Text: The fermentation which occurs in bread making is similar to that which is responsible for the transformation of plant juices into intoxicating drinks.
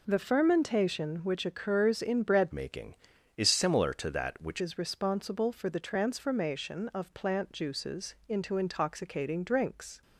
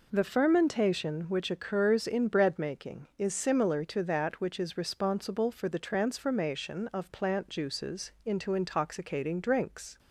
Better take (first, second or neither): second